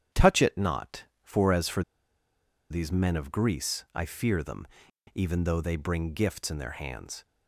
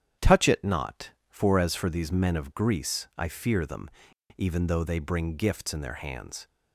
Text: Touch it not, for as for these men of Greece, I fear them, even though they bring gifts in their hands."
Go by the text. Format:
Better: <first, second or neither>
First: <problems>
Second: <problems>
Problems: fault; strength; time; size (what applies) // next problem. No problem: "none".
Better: second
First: starts louder than the rest; strong; until 1.3 s; 9.5 dB // pauses between "for" and "these"; noticeable; at 1.8 s; 0.88 s long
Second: starts louder than the rest; strong; until 1.3 s; 9.5 dB